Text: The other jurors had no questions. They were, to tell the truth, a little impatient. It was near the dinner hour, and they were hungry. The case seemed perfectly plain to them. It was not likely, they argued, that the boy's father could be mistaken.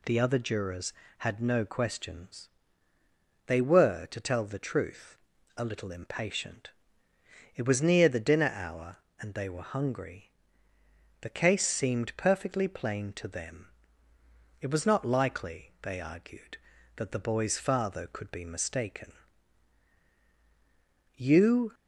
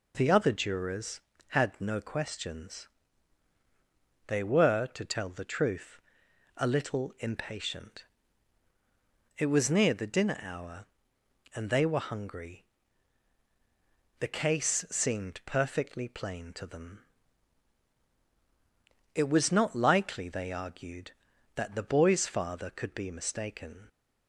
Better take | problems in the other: second | goes on to say "You"; from 21.1 s on; 0.58 s long

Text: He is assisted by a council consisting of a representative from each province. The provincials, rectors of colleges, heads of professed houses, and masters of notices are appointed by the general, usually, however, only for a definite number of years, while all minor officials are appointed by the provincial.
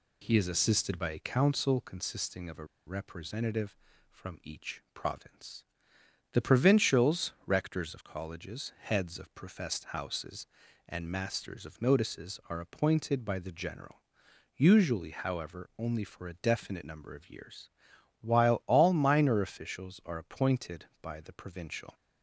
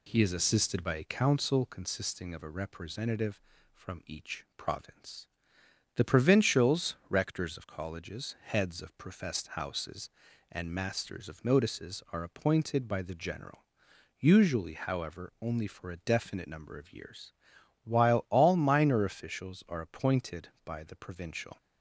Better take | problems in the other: second | pauses between "a" and "representative"; slight; at 2.6 s; 0.22 s long

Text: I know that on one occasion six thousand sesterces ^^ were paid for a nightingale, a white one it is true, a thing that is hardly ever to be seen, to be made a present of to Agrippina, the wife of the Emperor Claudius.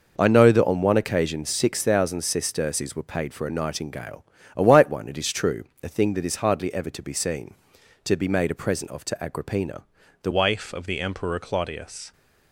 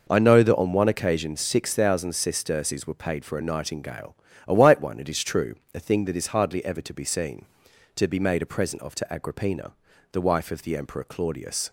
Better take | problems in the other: second | changes voice at "wife"; from 10.3 s on; 1.8 s long

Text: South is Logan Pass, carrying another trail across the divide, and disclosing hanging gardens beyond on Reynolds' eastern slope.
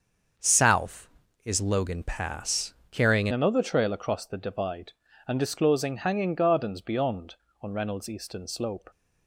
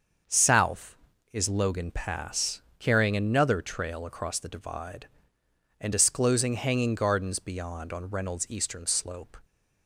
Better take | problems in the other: second | starts louder than the rest; until 1.7 s; 6.5 dB; also in the second // changes voice at "another"; from 3.3 s on; 5.6 s long

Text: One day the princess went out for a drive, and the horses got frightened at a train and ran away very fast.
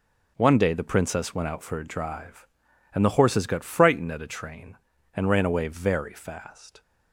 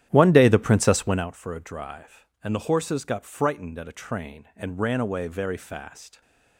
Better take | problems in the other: first | starts louder than the rest; strong; until 1.3 s; 11 dB

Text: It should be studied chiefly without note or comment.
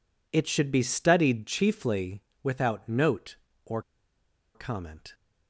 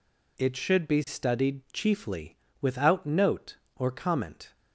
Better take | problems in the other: second | pauses between "chiefly" and "without"; slight; at 2.2 s; 0.20 s long; slight in the second // pauses between "or" and "comment"; noticeable; at 3.7 s; 0.74 s long

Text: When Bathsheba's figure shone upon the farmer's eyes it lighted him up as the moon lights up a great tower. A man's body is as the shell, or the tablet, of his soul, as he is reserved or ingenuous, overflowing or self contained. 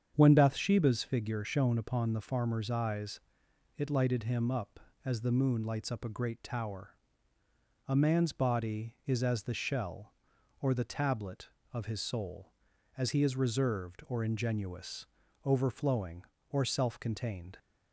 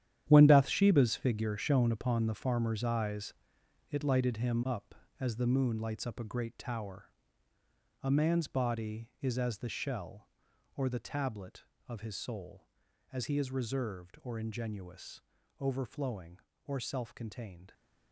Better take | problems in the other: first | gets quieter; strong; throughout; 12.5 dB // starts louder than the rest; strong; until 1.3 s; 10.5 dB; strong in the first // pauses between "eyes" and "it"; noticeable; at 3.3 s; 0.58 s long; noticeable in the first

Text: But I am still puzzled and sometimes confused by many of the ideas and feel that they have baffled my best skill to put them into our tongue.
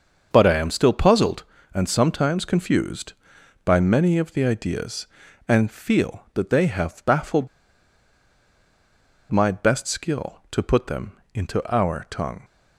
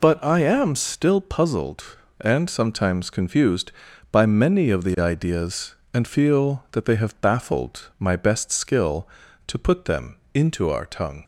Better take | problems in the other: second | starts louder than the rest; until 1.3 s; 6.5 dB // pauses between "baffled" and "my"; strong; at 7.4 s; 1.8 s long // pauses between "them" and "into"; slight; at 11.1 s; 0.20 s long; slight in the second

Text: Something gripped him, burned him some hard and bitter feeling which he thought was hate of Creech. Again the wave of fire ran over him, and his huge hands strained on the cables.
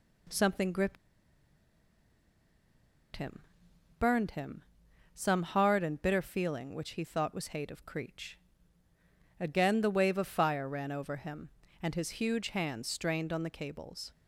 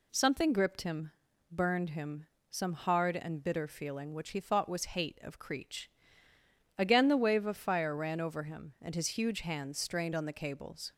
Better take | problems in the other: second | pauses between "gripped" and "him"; strong; at 0.9 s; 2.1 s long // pauses between "him" and "some"; noticeable; at 4.6 s; 0.54 s long; slight in the second

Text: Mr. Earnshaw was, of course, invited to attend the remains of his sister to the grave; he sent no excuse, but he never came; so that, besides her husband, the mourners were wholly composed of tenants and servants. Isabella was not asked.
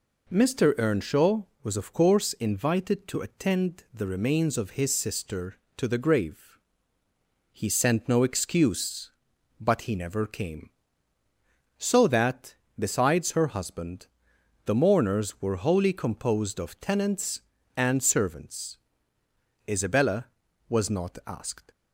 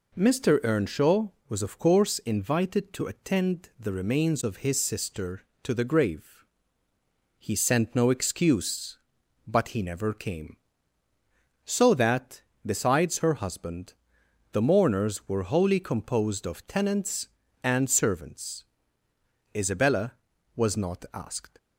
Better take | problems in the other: neither | none

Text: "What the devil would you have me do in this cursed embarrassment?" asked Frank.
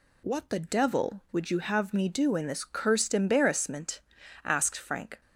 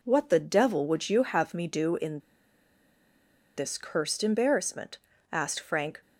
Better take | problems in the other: first | pauses between "in" and "this"; strong; at 2.1 s; 1.3 s long

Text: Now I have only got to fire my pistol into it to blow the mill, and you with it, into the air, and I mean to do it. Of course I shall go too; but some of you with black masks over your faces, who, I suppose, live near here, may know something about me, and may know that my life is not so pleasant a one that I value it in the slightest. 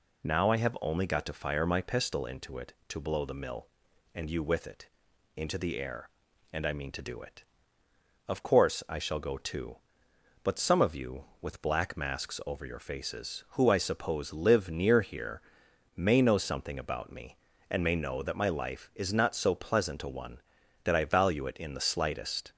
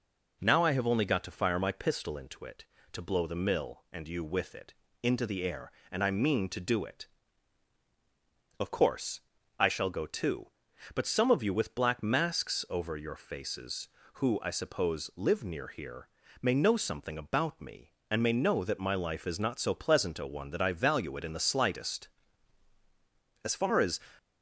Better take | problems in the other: first | pauses between "course" and "I"; at 9.2 s; 0.38 s long // goes on to say "As far as"; from 23.4 s on; 0.56 s long

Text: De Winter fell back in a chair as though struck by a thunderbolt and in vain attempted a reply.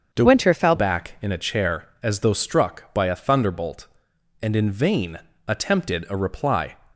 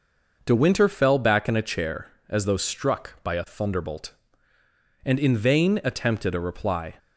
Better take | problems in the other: second | starts louder than the rest; until 1.1 s; 7 dB // changes voice from "Winter" to "fell"; from 0.2 to 0.7 s; 0.5 s long // pauses between "vain" and "attempted"; slight; at 5.1 s; 0.30 s long

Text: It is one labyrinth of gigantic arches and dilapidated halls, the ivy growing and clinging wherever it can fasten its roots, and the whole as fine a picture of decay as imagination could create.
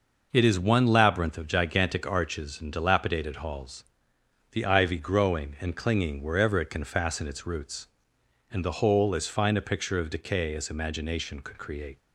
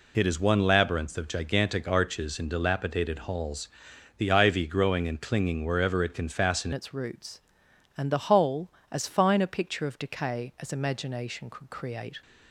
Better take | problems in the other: first | changes voice at "its"; from 6.7 s on; 5.5 s long

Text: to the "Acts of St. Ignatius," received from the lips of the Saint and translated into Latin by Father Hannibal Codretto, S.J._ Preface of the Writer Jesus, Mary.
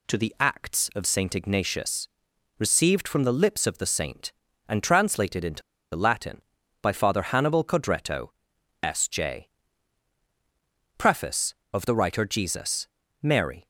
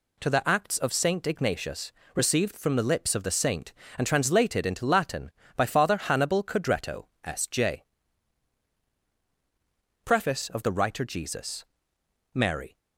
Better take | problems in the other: second | pauses between "into" and "Latin"; slight; at 5.6 s; 0.33 s long

